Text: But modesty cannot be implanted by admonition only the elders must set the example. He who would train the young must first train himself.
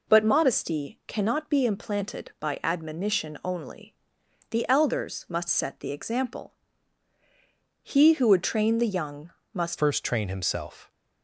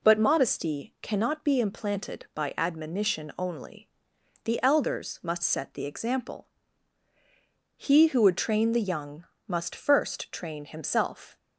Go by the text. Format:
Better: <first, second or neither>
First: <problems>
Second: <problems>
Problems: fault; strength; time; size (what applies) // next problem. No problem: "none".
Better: second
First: pauses between "only" and "the"; noticeable; at 3.9 s; 0.56 s long // pauses between "young" and "must"; slight; at 9.2 s; 0.24 s long // changes voice at "first"; from 9.7 s on; 1.2 s long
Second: pauses between "only" and "the"; noticeable; at 3.8 s; 0.56 s long // pauses between "young" and "must"; slight; at 9.2 s; 0.24 s long